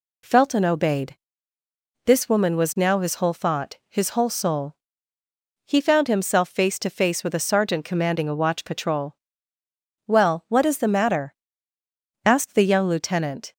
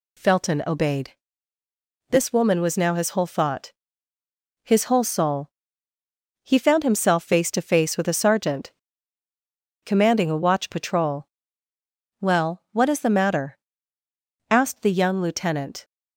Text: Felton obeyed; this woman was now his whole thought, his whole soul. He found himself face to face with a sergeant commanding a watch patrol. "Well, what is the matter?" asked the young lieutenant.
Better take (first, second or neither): first